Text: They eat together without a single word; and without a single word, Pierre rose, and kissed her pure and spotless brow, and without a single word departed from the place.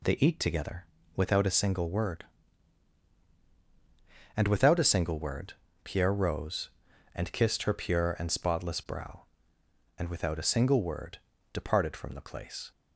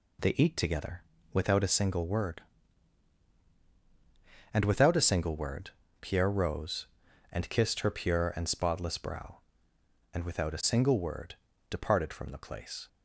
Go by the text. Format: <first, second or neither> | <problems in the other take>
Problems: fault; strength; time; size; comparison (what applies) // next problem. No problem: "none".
neither | pauses between "together" and "without"; slight; the same in both // pauses between "word" and "departed"; slight; the same in both